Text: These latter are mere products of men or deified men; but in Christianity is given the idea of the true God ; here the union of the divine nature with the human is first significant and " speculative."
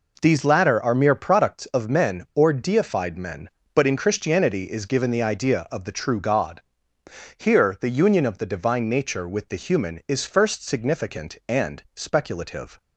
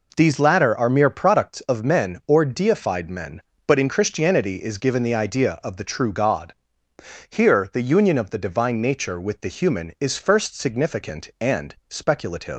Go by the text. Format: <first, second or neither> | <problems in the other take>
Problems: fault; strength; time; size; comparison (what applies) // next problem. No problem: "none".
first | leaves "speculative" unfinished; at 12.5 s; 165 ms